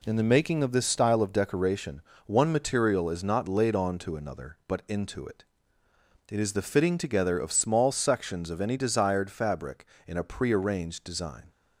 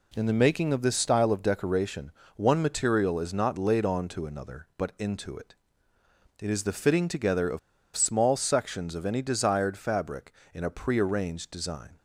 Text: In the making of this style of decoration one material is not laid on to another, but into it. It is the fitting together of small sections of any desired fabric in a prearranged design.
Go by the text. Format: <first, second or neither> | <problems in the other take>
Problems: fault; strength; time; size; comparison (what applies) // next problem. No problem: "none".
first | pauses between "decoration" and "one"; slight; at 2.1 s; 0.26 s long; slight in the first // pauses between "of" and "small"; at 7.5 s; 0.37 s long